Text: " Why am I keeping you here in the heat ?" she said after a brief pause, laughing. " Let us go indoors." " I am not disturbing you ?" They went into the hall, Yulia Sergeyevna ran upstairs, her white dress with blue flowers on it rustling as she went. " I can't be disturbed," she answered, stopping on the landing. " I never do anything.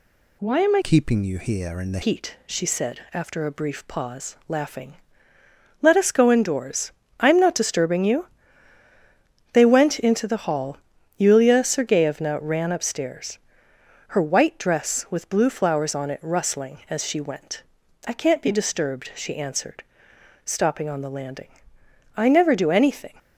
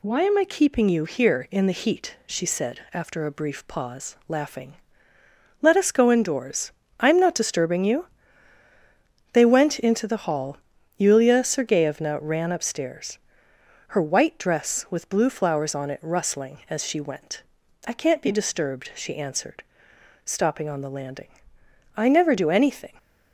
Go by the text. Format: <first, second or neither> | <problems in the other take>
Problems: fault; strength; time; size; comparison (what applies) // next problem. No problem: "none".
second | changes voice from "keeping" to "the"; from 0.8 to 2.0 s; 1.2 s long